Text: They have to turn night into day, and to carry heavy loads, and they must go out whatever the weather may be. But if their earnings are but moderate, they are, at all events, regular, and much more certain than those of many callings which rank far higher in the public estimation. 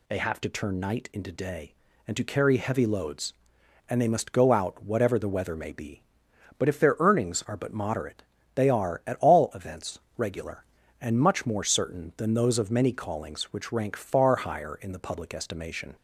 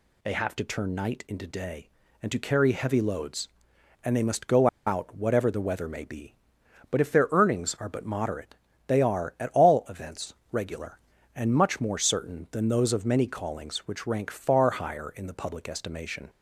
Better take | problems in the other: first | pauses between "go" and "out"; slight; at 4.6 s; 0.20 s long

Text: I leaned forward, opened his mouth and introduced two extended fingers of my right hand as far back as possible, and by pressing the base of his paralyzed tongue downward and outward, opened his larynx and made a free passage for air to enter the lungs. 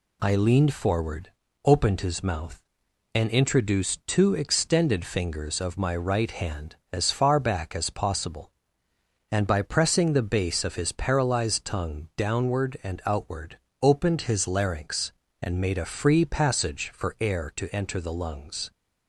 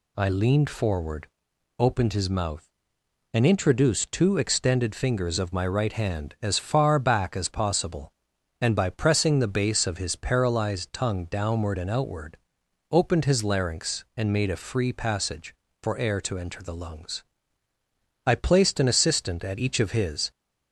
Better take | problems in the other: first | goes on to say "I placed an assistant at each of his"; strong; from 18.2 s on; 2.0 s long

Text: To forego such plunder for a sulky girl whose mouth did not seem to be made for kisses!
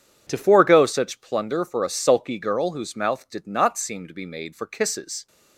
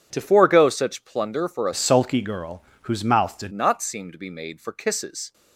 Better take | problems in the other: first | starts louder than the rest; strong; until 1.1 s; 8.5 dB // changes voice from "sulky" to "did"; from 1.7 to 3.5 s; 1.8 s long // pauses between "girl" and "whose"; slight; at 2.6 s; 0.20 s long

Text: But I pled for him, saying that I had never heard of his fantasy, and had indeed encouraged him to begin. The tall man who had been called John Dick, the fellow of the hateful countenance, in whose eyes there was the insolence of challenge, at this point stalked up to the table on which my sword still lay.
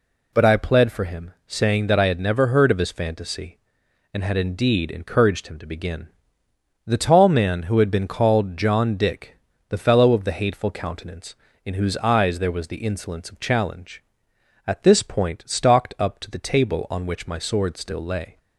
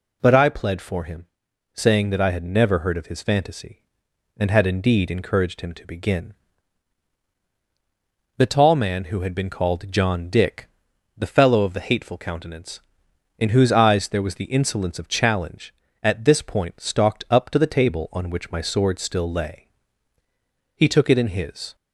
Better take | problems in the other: first | goes on to say "He took it in his"; noticeable; from 20.7 s on; 1.0 s long

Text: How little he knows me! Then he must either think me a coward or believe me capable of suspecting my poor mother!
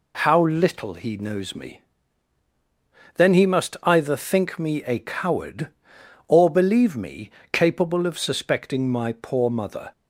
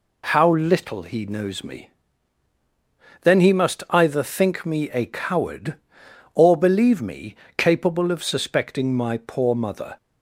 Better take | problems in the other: neither | pauses between "me" and "capable"; slight; the same in both

